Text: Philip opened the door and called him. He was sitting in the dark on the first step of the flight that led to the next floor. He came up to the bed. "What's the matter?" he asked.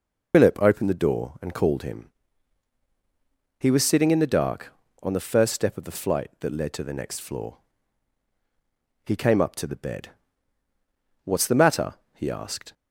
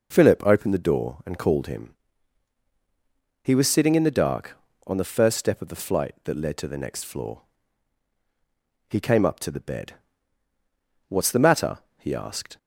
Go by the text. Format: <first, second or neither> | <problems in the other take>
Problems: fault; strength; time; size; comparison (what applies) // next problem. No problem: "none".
second | loses the start of "Philip"; at 0.3 s; 85 ms